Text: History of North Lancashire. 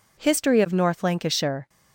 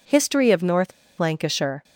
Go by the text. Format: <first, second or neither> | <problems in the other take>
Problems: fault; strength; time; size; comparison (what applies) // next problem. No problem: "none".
first | pauses between "North" and "Lancashire"; slight; at 0.9 s; 0.27 s long